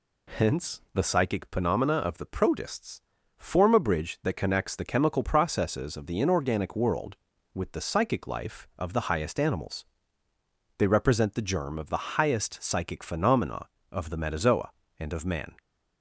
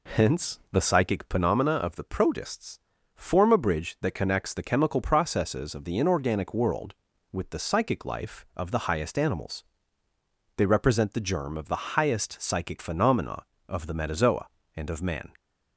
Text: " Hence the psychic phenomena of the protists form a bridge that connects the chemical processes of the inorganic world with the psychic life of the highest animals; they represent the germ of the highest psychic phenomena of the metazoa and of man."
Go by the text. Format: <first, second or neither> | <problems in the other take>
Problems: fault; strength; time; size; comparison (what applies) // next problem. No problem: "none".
first | starts louder than the rest; slight; until 1.8 s; 3 dB // pauses between "protists" and "form"; at 2.7 s; 0.38 s long; also in the first